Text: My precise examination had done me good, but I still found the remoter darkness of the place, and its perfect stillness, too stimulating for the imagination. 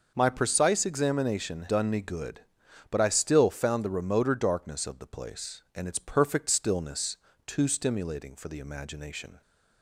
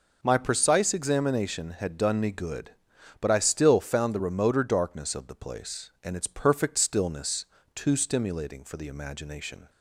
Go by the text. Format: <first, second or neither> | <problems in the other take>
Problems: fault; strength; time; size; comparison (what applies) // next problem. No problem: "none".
second | starts louder than the rest; until 1.1 s; 6 dB // skips "had"; at 1.6 s